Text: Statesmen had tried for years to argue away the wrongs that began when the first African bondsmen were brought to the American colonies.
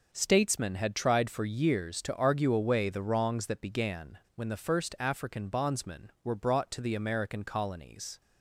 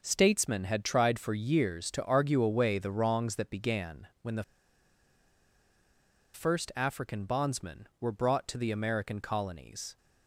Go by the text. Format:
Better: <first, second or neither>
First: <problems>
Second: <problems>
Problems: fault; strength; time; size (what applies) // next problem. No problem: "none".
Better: first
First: pauses between "began" and "when"; slight; at 4.1 s; 0.18 s long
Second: pauses between "began" and "when"; slight; at 4.0 s; 0.16 s long // pauses between "the" and "first"; strong; at 4.4 s; 1.9 s long